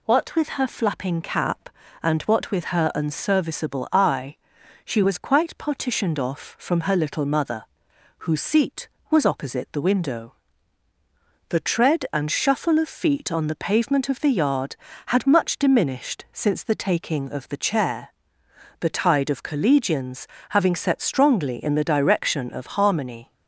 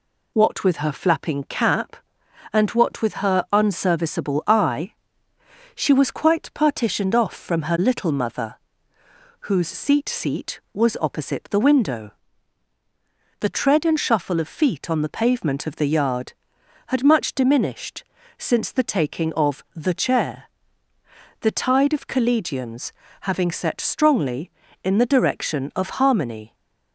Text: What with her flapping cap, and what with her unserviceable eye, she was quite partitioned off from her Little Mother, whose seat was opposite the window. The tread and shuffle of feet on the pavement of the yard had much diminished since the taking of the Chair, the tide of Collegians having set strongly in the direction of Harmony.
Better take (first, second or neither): first